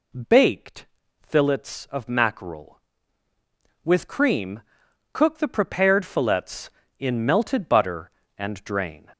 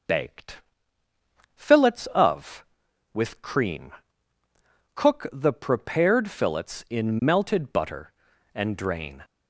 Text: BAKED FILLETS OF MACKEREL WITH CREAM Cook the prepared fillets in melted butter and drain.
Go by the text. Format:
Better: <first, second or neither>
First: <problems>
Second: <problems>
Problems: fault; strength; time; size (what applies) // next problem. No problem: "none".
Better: first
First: pauses between "BAKED" and "FILLETS"; slight; at 0.8 s; 0.36 s long // pauses between "CREAM" and "Cook"; noticeable; at 4.6 s; 0.52 s long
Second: pauses between "BAKED" and "FILLETS"; noticeable; at 0.5 s; 0.96 s long // skips "MACKEREL"; at 2.8 s // pauses between "CREAM" and "Cook"; at 3.9 s; 1.0 s long